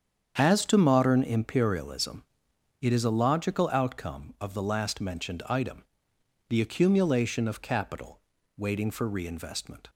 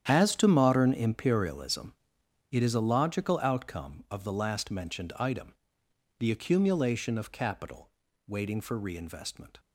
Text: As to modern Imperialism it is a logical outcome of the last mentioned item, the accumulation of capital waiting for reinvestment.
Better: first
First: starts louder than the rest; strong; until 1.3 s; 8 dB // pauses between "Imperialism" and "it"; noticeable; at 2.2 s; 0.60 s long // pauses between "capital" and "waiting"; at 8.2 s; 0.38 s long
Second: gets quieter; strong; throughout; 13.5 dB // starts louder than the rest; strong; until 1.0 s; 9.5 dB // pauses between "Imperialism" and "it"; noticeable; at 1.9 s; 0.60 s long // pauses between "capital" and "waiting"; at 7.9 s; 0.38 s long

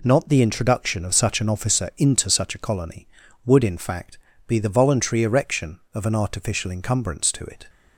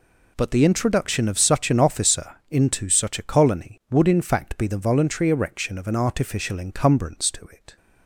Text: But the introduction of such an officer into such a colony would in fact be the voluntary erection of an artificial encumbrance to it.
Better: second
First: says "Not" for "But"; at 0.0 s // pauses between "fact" and "be"; slight; at 4.1 s; 0.30 s long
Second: none

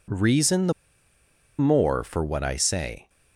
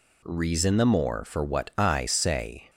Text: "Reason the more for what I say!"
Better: second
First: pauses between "the" and "more"; noticeable; at 0.7 s; 0.86 s long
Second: none

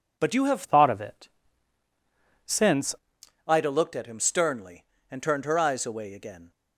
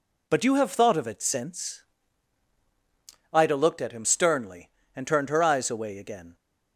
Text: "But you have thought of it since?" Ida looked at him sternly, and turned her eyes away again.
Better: second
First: changes voice from "thought" to "since"; from 0.6 to 2.9 s; 2.3 s long // pauses between "it" and "since"; at 1.2 s; 1.1 s long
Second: none

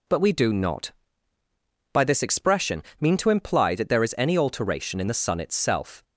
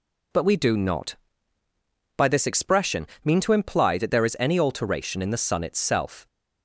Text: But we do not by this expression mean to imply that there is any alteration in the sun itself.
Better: neither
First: pauses between "expression" and "mean"; slight; at 2.8 s; 0.18 s long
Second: pauses between "expression" and "mean"; slight; at 3.0 s; 0.18 s long

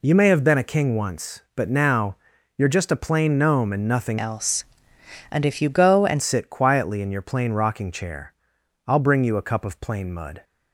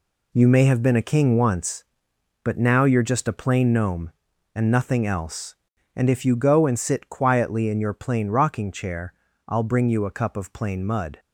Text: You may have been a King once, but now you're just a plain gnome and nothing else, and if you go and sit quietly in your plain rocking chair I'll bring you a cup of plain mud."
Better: second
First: pauses between "now" and "you're"; at 2.1 s; 0.40 s long // changes voice from "else" to "and"; from 4.1 to 6.2 s; 2.1 s long // pauses between "chair" and "I'll"; noticeable; at 8.3 s; 0.54 s long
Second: pauses between "chair" and "I'll"; slight; at 9.1 s; 0.34 s long

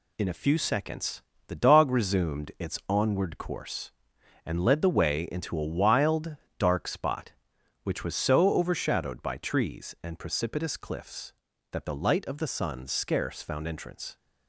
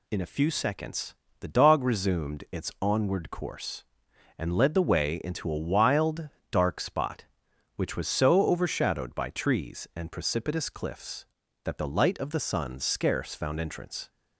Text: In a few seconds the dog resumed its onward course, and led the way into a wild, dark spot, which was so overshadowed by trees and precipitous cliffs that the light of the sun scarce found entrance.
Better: second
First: gets quieter; noticeable; throughout; 5 dB // pauses between "seconds" and "the"; slight; at 1.2 s; 0.26 s long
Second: pauses between "seconds" and "the"; slight; at 1.1 s; 0.26 s long

